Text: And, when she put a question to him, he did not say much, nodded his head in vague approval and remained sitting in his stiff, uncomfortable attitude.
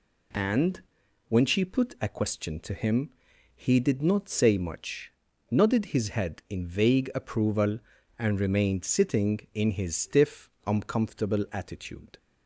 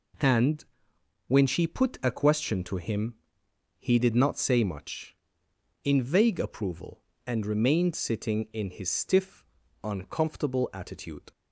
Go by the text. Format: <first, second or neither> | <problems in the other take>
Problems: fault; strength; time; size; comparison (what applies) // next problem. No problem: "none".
first | skips "nodded his head"; at 5.4 s